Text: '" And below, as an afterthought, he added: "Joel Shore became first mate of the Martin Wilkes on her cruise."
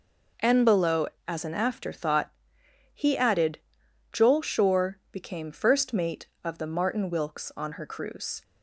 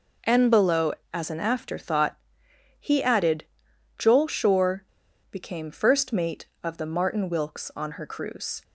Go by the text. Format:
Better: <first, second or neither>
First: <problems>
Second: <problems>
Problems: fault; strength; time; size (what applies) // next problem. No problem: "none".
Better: first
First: none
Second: pauses between "Shore" and "became"; noticeable; at 4.8 s; 0.47 s long